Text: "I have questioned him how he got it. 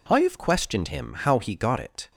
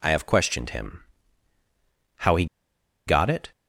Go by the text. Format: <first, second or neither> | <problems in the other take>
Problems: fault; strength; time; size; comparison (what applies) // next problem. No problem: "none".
first | pauses between "him" and "how"; at 1.0 s; 1.1 s long // pauses between "he" and "got"; noticeable; at 2.4 s; 0.62 s long